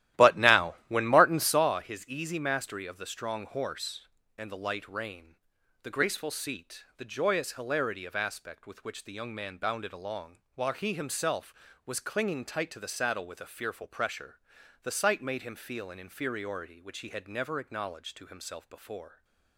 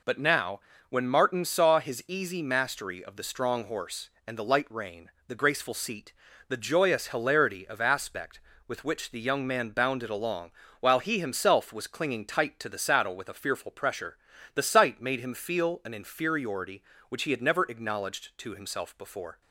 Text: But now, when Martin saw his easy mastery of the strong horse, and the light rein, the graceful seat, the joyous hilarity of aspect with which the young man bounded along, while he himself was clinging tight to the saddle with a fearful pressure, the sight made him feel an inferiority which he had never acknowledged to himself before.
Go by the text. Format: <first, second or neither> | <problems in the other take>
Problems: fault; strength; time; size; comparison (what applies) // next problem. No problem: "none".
second | starts louder than the rest; strong; until 1.6 s; 13.5 dB